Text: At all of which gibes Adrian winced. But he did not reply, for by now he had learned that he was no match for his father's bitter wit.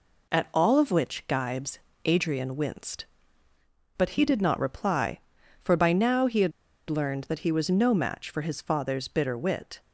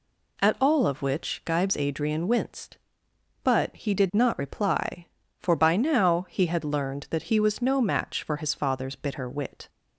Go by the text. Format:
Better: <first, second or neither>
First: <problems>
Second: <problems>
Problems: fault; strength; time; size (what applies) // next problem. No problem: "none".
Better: second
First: pauses between "gibes" and "Adrian"; slight; at 1.7 s; 0.26 s long // pauses between "had" and "learned"; at 6.5 s; 0.38 s long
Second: none